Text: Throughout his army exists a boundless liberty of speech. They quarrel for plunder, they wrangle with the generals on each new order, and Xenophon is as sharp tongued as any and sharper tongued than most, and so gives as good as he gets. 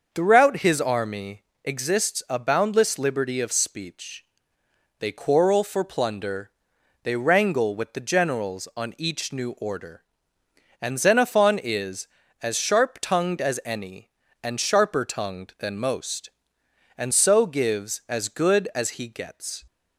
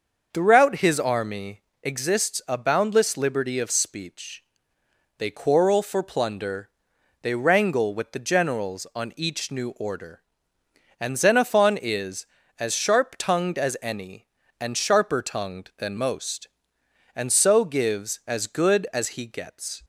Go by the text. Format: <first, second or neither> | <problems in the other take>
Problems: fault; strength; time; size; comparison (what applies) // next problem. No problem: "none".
neither | starts louder than the rest; the same in both // pauses between "army" and "exists"; slight; the same in both